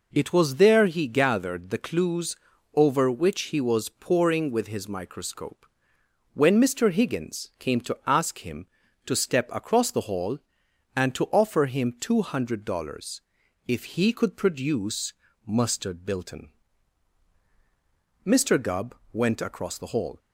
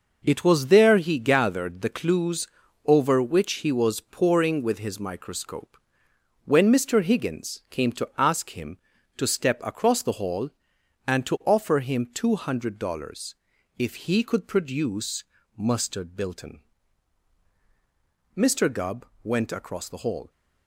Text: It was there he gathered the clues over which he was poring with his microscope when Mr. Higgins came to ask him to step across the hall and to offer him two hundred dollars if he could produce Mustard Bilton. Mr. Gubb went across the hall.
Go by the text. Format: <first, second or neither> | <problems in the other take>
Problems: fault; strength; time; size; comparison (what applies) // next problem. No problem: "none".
first | gets quieter; strong; throughout; 7.5 dB // pauses between "clues" and "over"; at 2.4 s; 0.38 s long; also in the first // pauses between "microscope" and "when"; noticeable; at 5.7 s; 0.68 s long; noticeable in the first // pauses between "dollars" and "if"; at 13.3 s; 0.42 s long; also in the first // pauses between "produce" and "Mustard"; slight; at 15.2 s; 0.32 s long; slight in the first // pauses between "Gubb" and "went"; slight; at 19.0 s; 0.18 s long; slight in the first